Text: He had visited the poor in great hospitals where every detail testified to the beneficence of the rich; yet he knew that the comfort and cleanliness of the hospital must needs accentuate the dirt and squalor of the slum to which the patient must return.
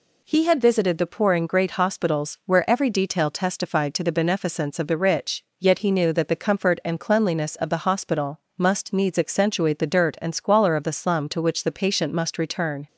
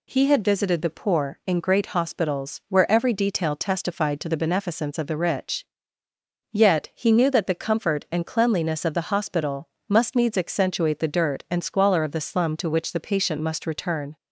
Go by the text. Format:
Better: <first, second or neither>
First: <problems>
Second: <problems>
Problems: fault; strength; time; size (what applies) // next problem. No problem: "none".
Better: neither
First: pauses between "hospital" and "must"; slight; at 8.3 s; 0.18 s long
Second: pauses between "hospital" and "must"; slight; at 9.6 s; 0.18 s long